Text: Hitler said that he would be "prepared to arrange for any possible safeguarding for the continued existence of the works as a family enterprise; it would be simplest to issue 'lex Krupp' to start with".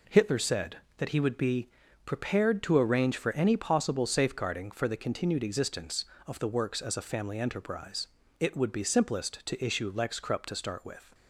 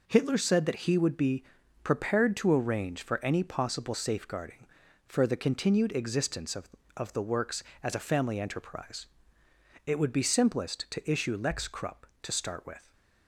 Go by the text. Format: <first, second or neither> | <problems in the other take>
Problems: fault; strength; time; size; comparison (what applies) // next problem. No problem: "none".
first | pauses between "be" and "prepared"; at 1.4 s; 0.38 s long; slight in the first // says "of" twice; at 6.9 s